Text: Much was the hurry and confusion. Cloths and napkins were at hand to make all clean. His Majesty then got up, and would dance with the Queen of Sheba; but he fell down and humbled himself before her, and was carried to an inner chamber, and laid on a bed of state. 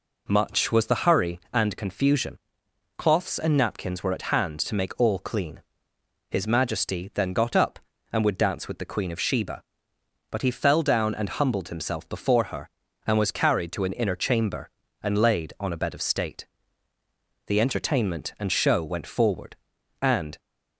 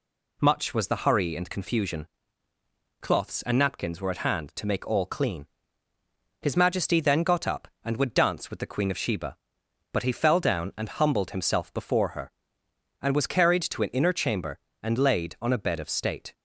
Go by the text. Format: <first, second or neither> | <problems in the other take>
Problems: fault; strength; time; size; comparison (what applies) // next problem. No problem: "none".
second | goes on to say "The entertainment and show went forward and"; strong; from 17.4 s on; 2.9 s long